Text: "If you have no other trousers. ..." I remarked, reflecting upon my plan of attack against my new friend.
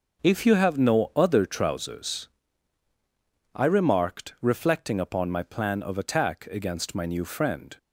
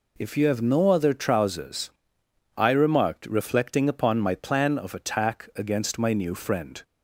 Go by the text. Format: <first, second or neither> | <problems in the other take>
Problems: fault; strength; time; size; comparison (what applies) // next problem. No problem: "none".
neither | none